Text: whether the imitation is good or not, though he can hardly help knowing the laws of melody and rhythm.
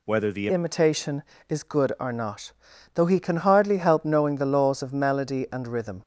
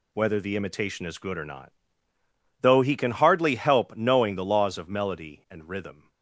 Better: second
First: changes voice at "imitation"; from 0.4 s on; 5.6 s long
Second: none

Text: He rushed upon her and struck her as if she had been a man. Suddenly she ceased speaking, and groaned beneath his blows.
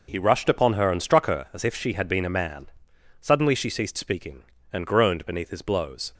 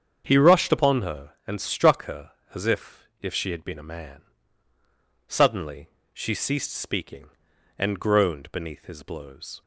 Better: first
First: none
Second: starts louder than the rest; strong; until 1.2 s; 7.5 dB // says "if" twice; at 3.2 s // pauses between "Suddenly" and "she"; slight; at 5.8 s; 0.26 s long

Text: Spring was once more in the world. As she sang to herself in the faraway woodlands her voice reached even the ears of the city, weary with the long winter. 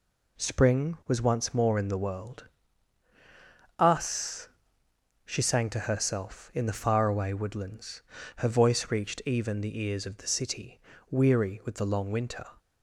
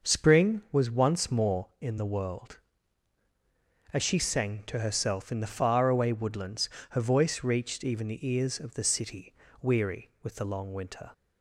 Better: second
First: says "Us" for "As"; at 3.8 s // pauses between "woodlands" and "her"; slight; at 8.0 s; 0.34 s long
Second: pauses between "woodlands" and "her"; slight; at 6.7 s; 0.20 s long

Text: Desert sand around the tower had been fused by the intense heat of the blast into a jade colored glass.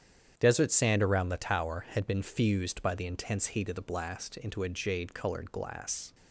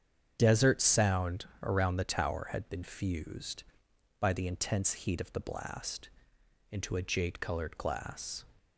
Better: first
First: starts louder than the rest; strong; until 1.3 s; 9 dB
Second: starts louder than the rest; strong; until 1.3 s; 8 dB // says "sound" for "sand"; at 0.8 s // pauses between "blast" and "into"; noticeable; at 6.0 s; 0.64 s long

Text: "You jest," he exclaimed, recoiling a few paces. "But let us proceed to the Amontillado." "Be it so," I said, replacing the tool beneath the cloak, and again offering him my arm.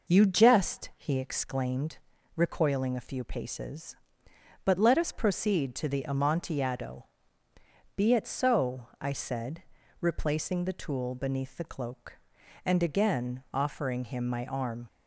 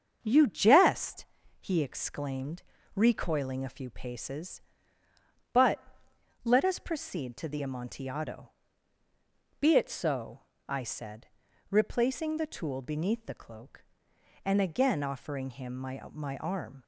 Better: first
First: none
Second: starts louder than the rest; until 1.2 s; 7 dB // pauses between "But" and "let"; noticeable; at 5.8 s; 0.62 s long // says "my" twice; at 16.1 s

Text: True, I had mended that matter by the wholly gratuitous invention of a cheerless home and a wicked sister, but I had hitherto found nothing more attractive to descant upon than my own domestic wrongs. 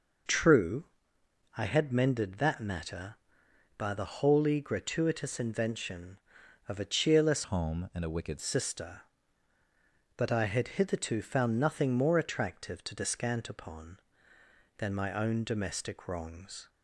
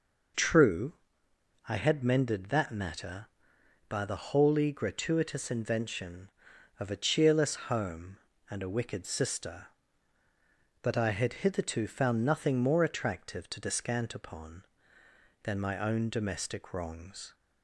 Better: second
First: changes voice from "home" to "wicked"; from 7.4 to 8.3 s; 0.9 s long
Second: none

